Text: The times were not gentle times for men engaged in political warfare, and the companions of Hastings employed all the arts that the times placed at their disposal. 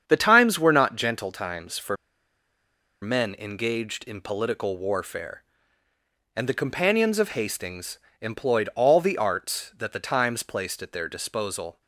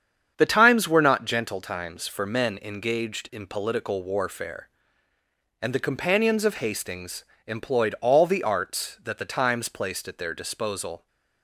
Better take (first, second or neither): second